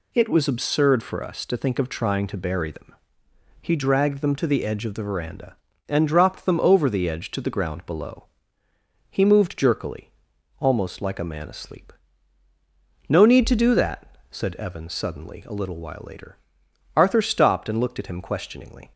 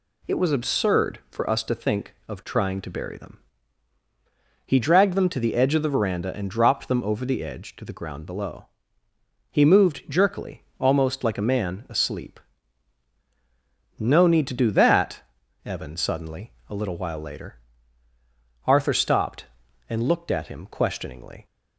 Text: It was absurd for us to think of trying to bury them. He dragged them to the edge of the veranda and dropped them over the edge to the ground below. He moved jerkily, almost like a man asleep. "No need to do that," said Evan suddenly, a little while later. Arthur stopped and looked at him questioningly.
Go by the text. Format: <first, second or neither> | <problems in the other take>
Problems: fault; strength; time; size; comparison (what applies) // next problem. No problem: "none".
first | skips "said"; at 15.4 s